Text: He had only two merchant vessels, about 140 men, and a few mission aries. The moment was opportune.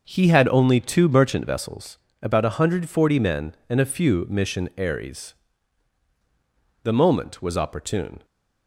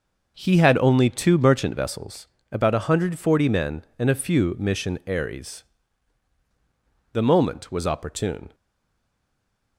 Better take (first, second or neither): first